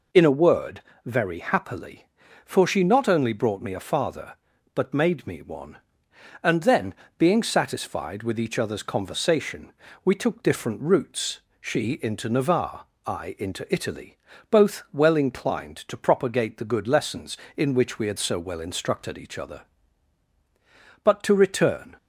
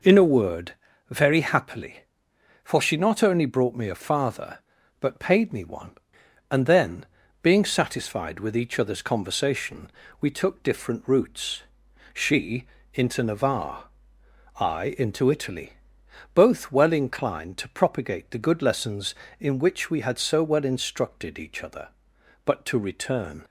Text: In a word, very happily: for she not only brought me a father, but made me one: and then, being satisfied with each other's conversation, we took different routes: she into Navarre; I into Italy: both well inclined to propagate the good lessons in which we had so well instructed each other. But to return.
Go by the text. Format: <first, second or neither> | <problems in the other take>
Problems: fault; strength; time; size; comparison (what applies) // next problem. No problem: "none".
first | says "paid" for "made"; at 5.1 s // pauses between "she" and "into"; slight; at 12.6 s; 0.30 s long